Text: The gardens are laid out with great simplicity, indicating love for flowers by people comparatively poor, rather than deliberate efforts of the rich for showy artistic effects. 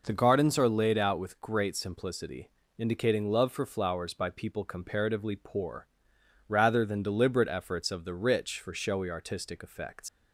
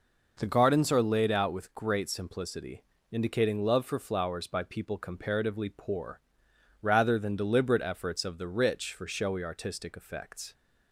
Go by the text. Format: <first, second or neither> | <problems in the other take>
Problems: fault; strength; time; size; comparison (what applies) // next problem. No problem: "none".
second | leaves "effects" unfinished; at 10.0 s; 115 ms